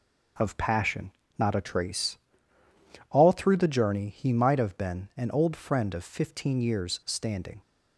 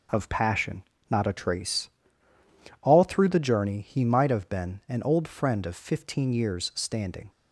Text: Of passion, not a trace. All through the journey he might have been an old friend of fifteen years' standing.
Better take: neither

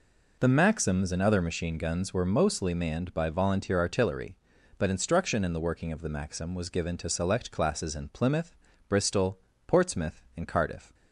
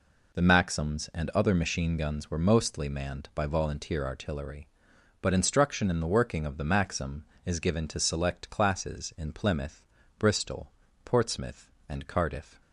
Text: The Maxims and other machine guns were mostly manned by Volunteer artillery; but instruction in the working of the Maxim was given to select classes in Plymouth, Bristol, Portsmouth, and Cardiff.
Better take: first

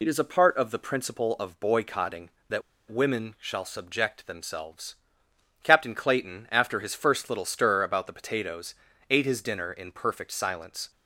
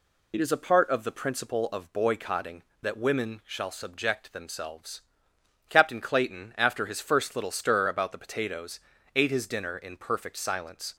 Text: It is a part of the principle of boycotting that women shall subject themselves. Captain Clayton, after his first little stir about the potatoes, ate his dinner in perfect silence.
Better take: second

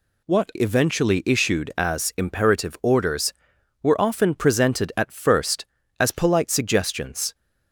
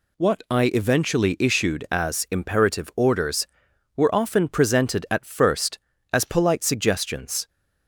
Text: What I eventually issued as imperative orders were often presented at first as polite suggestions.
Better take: second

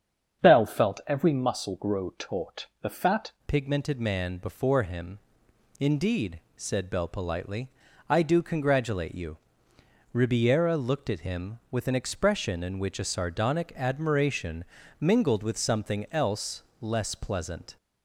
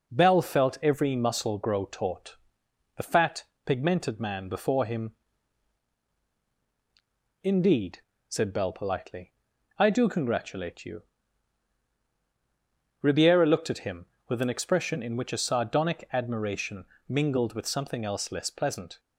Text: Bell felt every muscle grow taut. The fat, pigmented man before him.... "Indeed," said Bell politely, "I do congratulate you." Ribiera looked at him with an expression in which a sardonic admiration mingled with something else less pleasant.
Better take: second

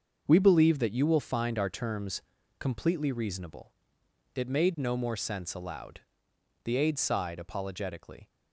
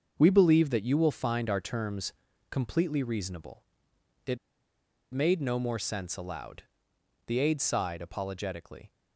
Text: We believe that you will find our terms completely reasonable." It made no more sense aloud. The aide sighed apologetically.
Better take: first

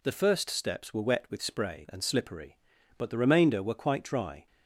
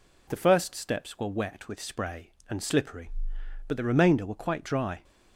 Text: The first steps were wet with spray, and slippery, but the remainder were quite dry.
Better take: neither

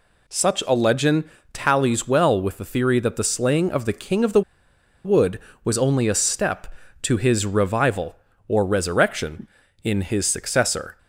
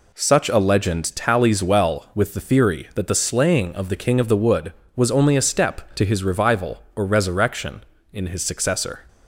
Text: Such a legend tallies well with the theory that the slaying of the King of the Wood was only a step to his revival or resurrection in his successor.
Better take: second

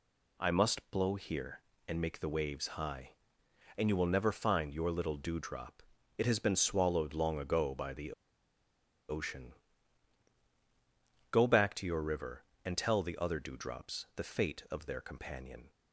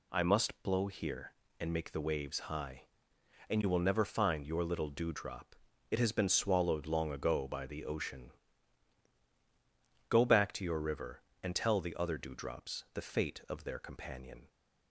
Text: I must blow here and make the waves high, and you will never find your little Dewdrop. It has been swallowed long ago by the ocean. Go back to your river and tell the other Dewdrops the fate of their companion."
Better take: second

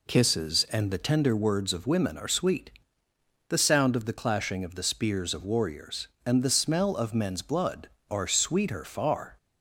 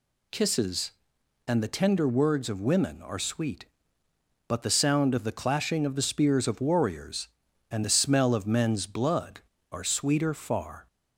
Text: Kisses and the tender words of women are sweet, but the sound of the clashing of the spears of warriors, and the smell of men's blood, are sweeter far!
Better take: second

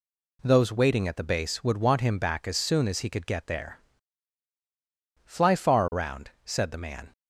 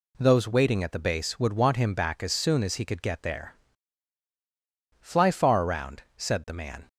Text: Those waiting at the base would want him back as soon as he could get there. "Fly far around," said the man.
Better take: neither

